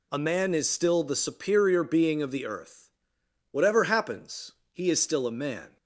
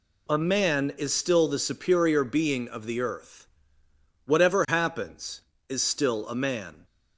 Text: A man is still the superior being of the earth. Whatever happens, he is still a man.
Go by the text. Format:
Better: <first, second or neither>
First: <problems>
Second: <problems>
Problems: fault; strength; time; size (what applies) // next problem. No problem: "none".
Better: first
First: none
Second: skips "he"; at 5.5 s